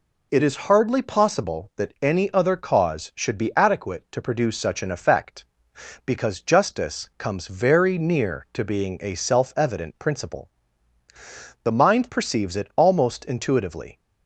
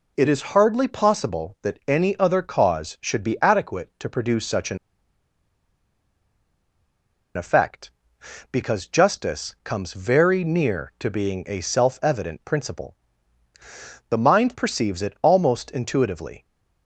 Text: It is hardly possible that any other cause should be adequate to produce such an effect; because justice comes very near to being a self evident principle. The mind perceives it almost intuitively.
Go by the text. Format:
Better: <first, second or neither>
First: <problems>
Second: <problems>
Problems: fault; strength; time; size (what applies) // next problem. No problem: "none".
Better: first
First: none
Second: pauses between "an" and "effect"; strong; at 4.7 s; 2.5 s long